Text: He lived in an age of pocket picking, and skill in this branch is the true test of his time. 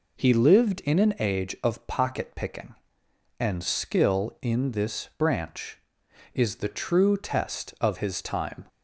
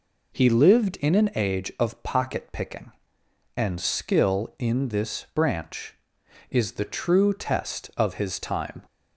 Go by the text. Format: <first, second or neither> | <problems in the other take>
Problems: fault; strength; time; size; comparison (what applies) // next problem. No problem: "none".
neither | none